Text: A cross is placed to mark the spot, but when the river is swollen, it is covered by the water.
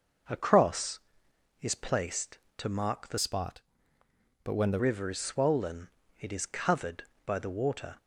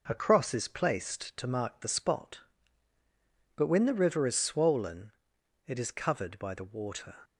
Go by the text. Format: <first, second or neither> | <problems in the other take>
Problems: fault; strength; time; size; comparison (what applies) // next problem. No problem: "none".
second | changes voice from "spot" to "the"; from 3.1 to 4.7 s; 1.6 s long